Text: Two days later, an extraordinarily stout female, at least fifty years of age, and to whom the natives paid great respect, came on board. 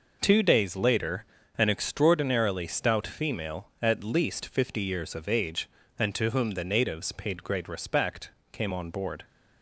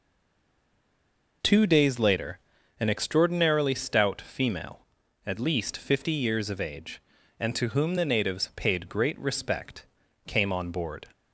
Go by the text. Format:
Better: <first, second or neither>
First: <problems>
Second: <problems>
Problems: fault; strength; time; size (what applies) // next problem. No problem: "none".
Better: first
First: none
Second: stays silent before the first word; noticeable; until 1.4 s; 1.4 s long